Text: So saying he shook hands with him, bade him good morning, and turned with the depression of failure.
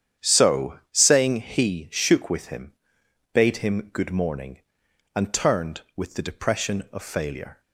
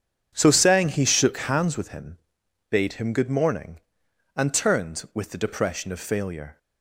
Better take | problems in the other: second | starts louder than the rest; strong; until 1.3 s; 9 dB; strong in the second // skips "hands"; at 2.2 s

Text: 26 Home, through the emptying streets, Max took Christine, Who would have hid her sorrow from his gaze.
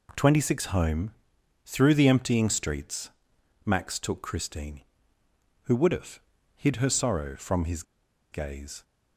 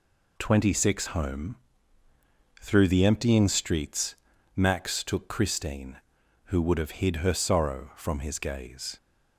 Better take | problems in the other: second | pauses between "have" and "hid"; slight; at 6.2 s; 0.36 s long // pauses between "his" and "gaze"; noticeable; at 7.8 s; 0.49 s long

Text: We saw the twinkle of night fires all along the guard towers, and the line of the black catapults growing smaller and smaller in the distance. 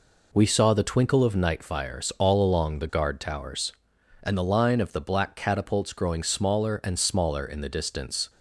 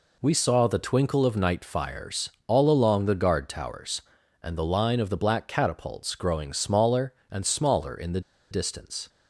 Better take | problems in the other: first | pauses between "fires" and "all"; slight; at 2.3 s; 0.18 s long // pauses between "the" and "distance"; slight; at 8.2 s; 0.30 s long

